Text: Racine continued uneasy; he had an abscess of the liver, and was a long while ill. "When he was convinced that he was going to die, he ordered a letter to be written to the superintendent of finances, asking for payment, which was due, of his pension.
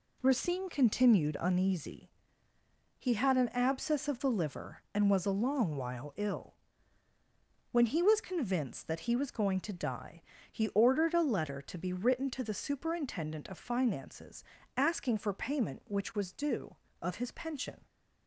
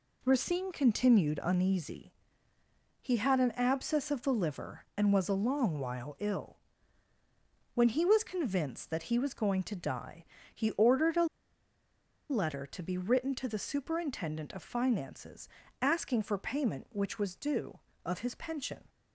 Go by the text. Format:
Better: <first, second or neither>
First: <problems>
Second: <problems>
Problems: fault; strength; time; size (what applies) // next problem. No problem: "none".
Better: first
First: none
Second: pauses between "a" and "letter"; at 11.2 s; 1.0 s long